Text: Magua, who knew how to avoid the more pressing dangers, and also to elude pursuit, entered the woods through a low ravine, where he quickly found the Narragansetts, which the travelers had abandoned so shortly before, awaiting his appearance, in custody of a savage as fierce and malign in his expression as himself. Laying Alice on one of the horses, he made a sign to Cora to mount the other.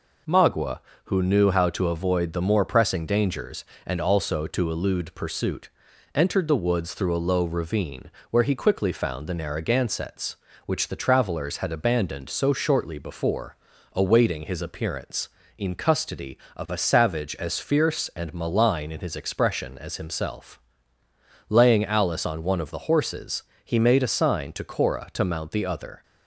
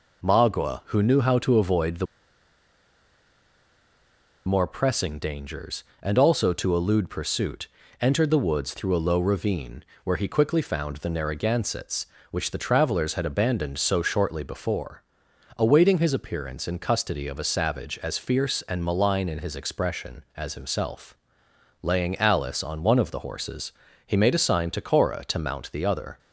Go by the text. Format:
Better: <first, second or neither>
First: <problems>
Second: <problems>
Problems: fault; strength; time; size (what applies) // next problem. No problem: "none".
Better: first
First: none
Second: pauses between "the" and "more"; strong; at 2.0 s; 2.4 s long